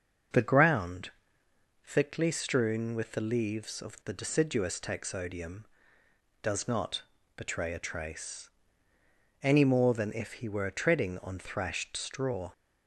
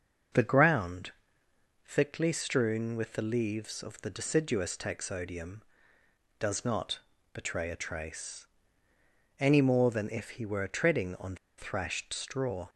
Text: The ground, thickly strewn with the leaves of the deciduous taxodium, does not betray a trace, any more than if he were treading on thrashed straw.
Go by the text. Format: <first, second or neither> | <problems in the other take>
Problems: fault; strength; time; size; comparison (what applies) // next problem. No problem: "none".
first | starts louder than the rest; until 2.0 s; 6.5 dB; also in the first // pauses between "not" and "betray"; slight; at 7.0 s; 0.34 s long; slight in the first // pauses between "on" and "thrashed"; slight; at 11.3 s; 0.21 s long